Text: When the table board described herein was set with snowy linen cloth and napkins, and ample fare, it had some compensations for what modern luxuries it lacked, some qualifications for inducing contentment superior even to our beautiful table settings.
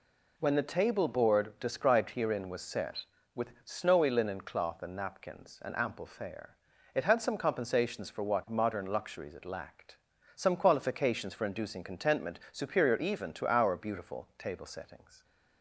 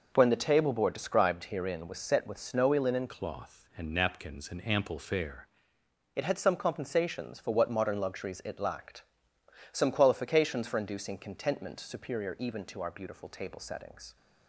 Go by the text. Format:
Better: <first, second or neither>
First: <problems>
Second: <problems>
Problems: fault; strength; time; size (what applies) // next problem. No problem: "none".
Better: first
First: none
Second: changes voice from "cloth" to "fare"; from 3.0 to 5.4 s; 2.4 s long